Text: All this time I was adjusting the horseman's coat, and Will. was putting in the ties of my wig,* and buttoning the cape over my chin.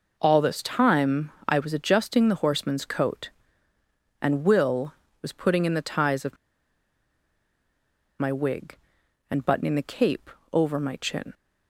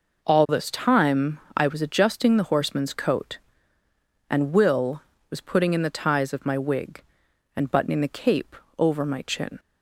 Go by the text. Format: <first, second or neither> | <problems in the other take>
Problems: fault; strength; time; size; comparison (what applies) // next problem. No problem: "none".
second | pauses between "time" and "I"; slight; at 1.3 s; 0.16 s long; slight in the second // pauses between "of" and "my"; strong; at 6.3 s; 1.8 s long // pauses between "cape" and "over"; slight; at 10.2 s; 0.24 s long; slight in the second